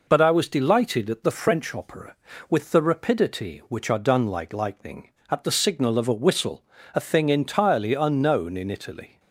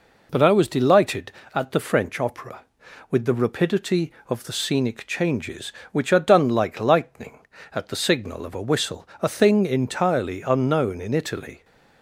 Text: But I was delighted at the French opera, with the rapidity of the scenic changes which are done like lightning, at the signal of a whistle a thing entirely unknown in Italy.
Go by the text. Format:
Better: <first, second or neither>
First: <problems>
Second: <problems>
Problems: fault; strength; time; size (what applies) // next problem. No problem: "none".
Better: second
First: skips "of the scenic changes"; at 3.6 s // pauses between "whistle" and "a"; slight; at 6.6 s; 0.32 s long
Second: none